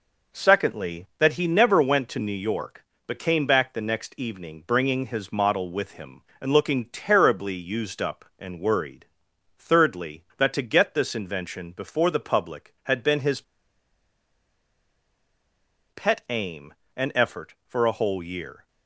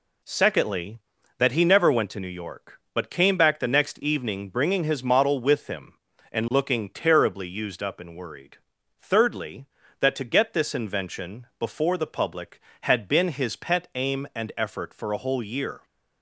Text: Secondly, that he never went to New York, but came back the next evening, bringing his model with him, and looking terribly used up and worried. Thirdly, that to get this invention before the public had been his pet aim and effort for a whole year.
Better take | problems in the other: second | pauses between "his" and "pet"; strong; at 13.4 s; 2.4 s long

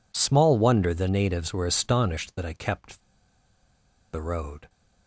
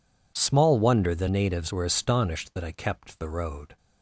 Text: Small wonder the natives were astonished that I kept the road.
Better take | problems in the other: second | pauses between "kept" and "the"; at 3.0 s; 1.1 s long

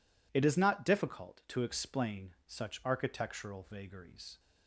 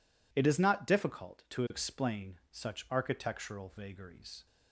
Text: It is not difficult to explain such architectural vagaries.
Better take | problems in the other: neither | none

